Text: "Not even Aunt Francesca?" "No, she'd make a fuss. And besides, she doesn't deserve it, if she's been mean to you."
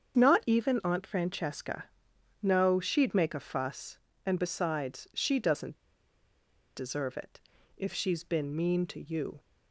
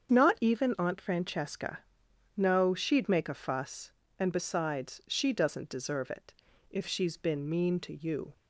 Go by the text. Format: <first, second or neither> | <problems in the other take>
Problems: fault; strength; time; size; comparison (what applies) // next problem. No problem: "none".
second | starts louder than the rest; strong; until 1.2 s; 7.5 dB; strong in the second // pauses between "doesn't" and "deserve"; at 5.7 s; 0.99 s long